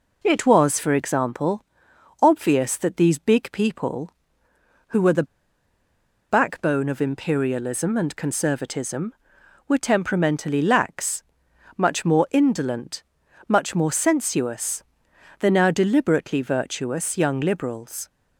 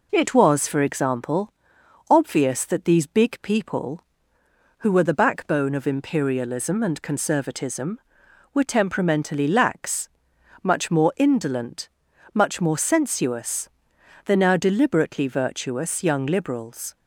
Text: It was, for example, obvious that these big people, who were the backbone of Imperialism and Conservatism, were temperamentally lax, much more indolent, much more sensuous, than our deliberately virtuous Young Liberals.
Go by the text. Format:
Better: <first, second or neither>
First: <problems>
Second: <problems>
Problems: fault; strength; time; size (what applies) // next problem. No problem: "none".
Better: second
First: pauses between "the" and "backbone"; at 5.2 s; 1.0 s long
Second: none